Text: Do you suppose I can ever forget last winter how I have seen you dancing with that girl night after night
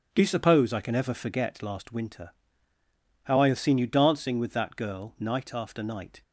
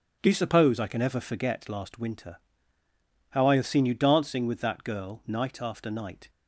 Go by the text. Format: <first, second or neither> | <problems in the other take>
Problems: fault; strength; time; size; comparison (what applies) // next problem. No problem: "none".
neither | starts louder than the rest; the same in both // pauses between "winter" and "how"; noticeable; the same in both